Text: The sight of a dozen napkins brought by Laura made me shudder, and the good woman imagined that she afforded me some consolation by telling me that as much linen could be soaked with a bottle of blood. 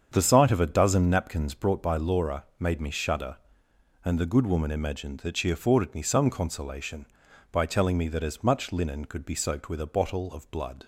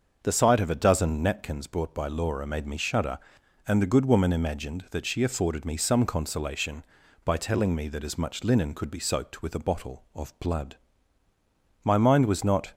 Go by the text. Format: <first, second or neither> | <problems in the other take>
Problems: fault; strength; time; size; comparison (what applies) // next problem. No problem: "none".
first | starts louder than the rest; until 1.2 s; 6.5 dB; strong in the first // goes on to say "My mind was not"; noticeable; from 11.8 s on; 0.90 s long